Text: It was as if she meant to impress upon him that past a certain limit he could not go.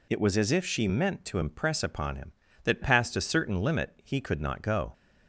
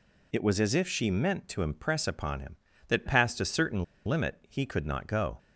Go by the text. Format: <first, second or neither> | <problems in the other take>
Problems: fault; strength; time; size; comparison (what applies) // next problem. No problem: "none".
first | pauses between "certain" and "limit"; slight; at 3.8 s; 0.21 s long